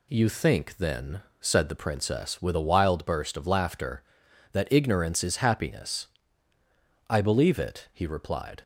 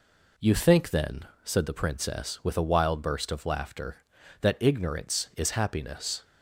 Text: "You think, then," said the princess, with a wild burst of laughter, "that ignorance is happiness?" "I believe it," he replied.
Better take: first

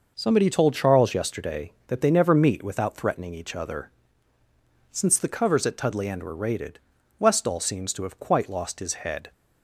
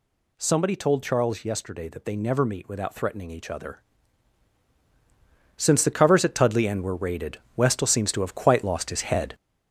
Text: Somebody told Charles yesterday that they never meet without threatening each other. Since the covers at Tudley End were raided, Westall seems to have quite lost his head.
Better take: first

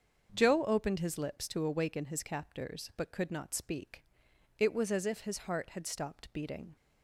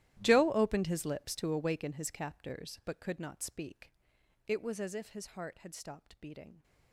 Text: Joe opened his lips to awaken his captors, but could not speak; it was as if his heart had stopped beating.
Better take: first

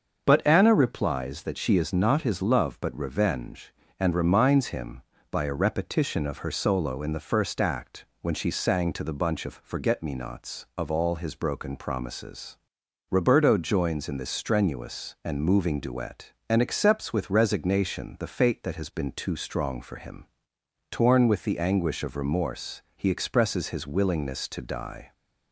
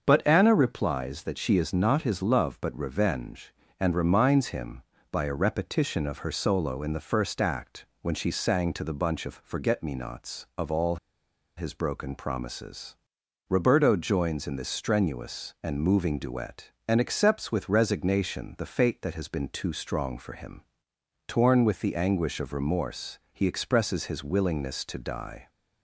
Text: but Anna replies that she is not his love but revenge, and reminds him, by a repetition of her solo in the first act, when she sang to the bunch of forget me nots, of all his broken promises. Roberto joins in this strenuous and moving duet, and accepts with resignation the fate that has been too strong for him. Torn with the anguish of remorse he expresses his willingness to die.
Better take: first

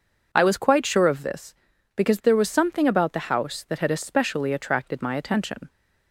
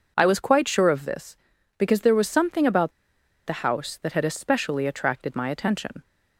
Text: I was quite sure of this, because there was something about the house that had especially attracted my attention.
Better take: first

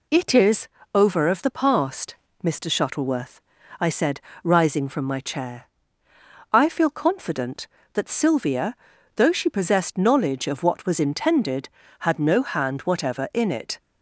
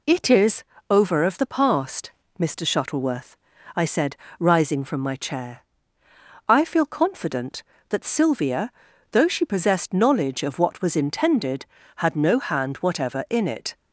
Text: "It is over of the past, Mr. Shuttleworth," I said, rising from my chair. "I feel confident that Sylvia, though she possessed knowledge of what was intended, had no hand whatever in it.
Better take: neither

